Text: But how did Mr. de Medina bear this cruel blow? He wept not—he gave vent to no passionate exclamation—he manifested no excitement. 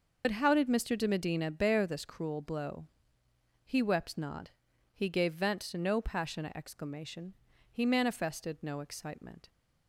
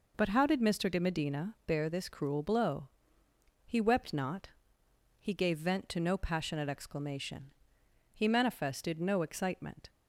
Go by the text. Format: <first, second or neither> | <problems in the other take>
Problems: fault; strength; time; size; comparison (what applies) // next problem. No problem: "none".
second | loses the start of "But"; at 0.2 s; 65 ms